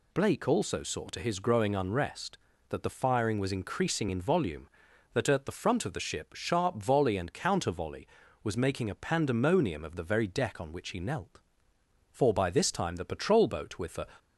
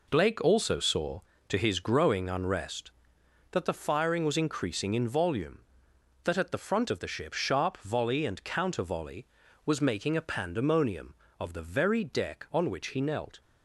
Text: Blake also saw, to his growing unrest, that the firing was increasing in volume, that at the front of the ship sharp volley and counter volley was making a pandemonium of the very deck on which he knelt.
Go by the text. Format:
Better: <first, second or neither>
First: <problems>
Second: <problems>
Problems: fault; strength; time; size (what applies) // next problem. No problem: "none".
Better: second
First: goes on to say "For by this time the patrol boat with the"; strong; from 12.0 s on; 1.9 s long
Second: none